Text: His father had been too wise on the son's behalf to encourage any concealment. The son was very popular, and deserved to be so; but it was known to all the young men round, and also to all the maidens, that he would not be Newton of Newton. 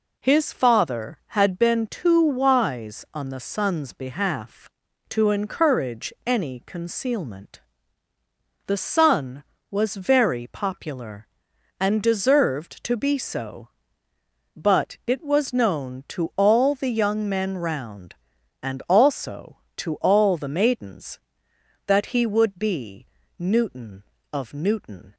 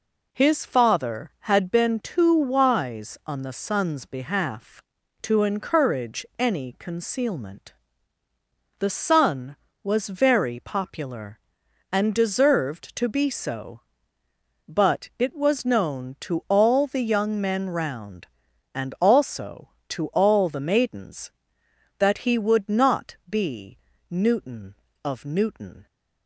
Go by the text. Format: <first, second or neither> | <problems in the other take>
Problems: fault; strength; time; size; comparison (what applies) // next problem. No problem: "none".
second | skips "not"; at 22.5 s // pauses between "be" and "Newton"; slight; at 23.0 s; 0.32 s long; slight in the second